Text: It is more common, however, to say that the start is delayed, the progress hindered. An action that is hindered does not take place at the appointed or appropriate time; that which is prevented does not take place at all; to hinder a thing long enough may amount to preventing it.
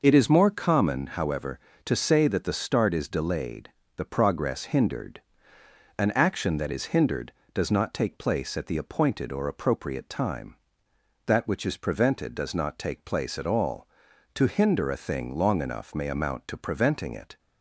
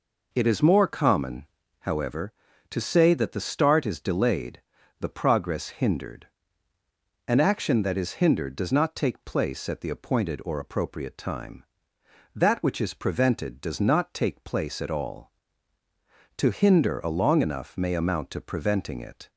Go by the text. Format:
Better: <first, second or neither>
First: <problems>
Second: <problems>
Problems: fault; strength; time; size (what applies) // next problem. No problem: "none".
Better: first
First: none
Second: skips "thing"; at 17.0 s